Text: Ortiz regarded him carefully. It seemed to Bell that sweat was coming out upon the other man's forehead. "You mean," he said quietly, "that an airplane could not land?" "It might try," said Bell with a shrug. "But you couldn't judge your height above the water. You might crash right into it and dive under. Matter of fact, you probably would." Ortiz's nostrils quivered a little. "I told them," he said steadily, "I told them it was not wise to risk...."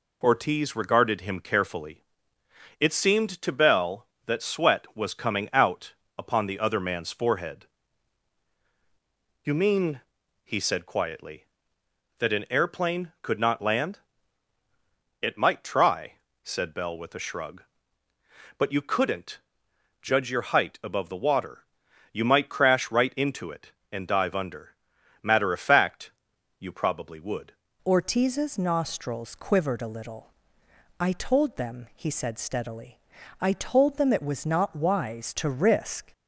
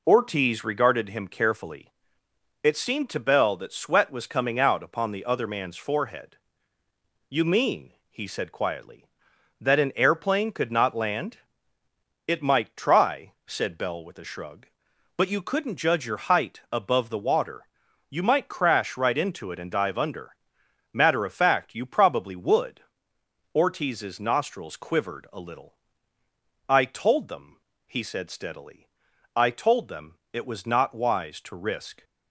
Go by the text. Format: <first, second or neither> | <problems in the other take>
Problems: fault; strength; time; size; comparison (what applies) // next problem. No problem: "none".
second | pauses between "out" and "upon"; slight; at 5.9 s; 0.24 s long // pauses between "couldn't" and "judge"; noticeable; at 19.3 s; 0.60 s long // changes voice at "Ortiz's"; from 27.8 s on; 8.3 s long